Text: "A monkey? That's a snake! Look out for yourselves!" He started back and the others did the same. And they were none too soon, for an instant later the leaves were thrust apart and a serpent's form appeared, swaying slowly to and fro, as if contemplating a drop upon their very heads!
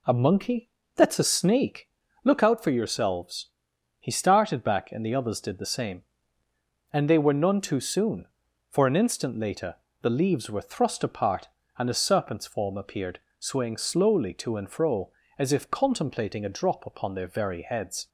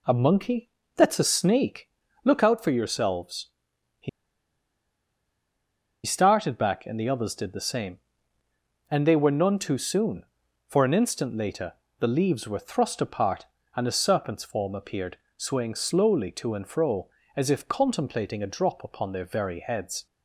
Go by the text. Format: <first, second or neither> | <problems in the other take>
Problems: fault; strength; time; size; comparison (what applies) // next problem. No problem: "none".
first | pauses between "He" and "started"; strong; at 4.0 s; 1.9 s long // pauses between "later" and "the"; slight; at 11.7 s; 0.24 s long; slight in the first